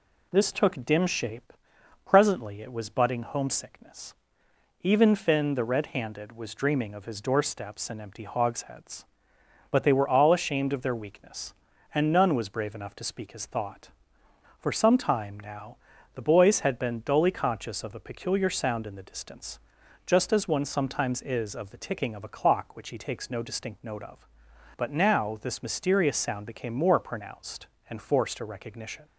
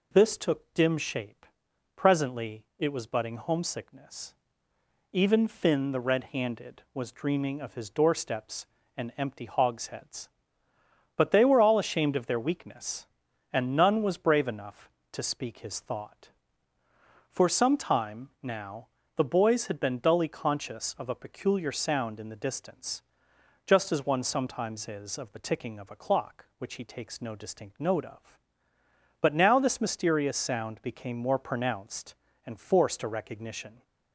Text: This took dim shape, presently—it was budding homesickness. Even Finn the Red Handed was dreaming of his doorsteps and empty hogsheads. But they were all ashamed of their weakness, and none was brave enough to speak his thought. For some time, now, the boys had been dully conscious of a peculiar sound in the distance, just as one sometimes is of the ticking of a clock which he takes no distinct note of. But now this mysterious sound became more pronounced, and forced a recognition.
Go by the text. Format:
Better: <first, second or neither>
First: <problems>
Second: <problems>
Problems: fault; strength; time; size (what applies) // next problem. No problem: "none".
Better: neither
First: none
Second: none